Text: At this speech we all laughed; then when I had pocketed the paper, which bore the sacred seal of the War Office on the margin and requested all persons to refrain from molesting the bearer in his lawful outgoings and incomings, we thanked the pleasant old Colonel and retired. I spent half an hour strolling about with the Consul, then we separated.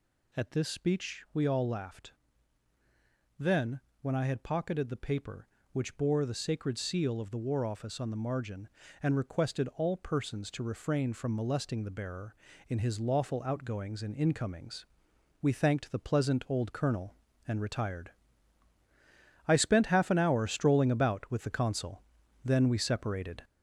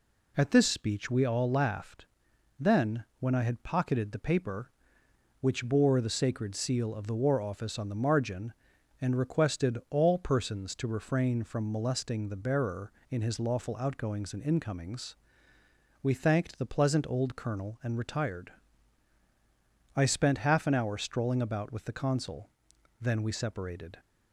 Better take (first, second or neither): second